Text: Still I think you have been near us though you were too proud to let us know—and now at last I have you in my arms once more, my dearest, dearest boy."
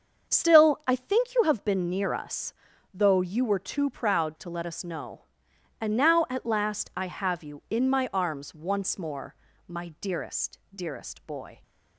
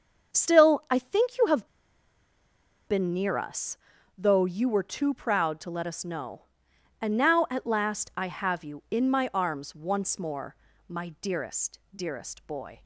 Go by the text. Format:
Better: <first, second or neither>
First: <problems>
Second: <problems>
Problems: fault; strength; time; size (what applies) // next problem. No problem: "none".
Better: first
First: starts louder than the rest; until 1.3 s; 6.5 dB // pauses between "us" and "though"; at 2.5 s; 0.40 s long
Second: starts louder than the rest; until 1.3 s; 6.5 dB // pauses between "have" and "been"; at 1.6 s; 1.2 s long // pauses between "us" and "though"; at 3.7 s; 0.40 s long